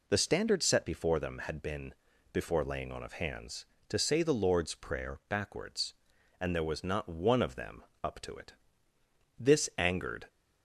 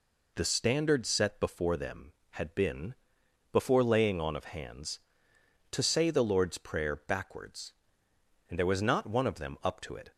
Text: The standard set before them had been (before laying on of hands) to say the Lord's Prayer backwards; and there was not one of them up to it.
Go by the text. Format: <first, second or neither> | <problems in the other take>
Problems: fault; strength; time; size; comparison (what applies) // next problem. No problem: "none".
second | pauses between "them" and "up"; slight; at 7.8 s; 0.22 s long // goes on to say "This angered"; noticeable; from 9.3 s on; 0.92 s long